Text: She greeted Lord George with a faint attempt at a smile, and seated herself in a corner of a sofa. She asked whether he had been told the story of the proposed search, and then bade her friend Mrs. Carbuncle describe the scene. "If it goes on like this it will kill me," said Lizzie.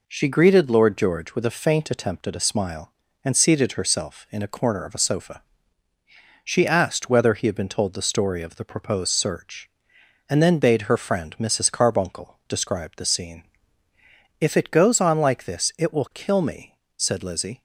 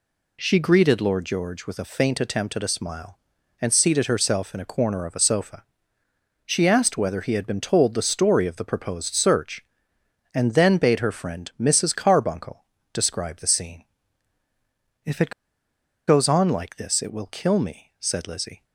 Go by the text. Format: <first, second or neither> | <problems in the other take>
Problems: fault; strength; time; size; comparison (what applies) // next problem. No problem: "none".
first | pauses between "Carbuncle" and "describe"; slight; at 12.6 s; 0.30 s long // pauses between "it" and "goes"; noticeable; at 15.3 s; 0.76 s long